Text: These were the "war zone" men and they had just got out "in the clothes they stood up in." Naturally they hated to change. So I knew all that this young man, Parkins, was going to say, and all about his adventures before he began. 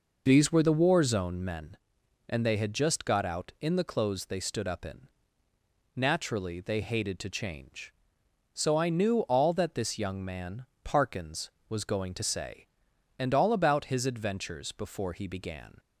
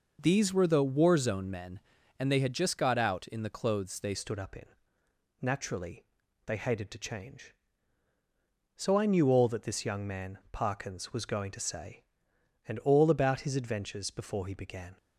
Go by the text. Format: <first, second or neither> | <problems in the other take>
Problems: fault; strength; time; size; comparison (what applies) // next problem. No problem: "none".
first | changes voice at "stood"; from 4.1 s on; 10.8 s long // pauses between "Naturally" and "they"; at 6.0 s; 0.44 s long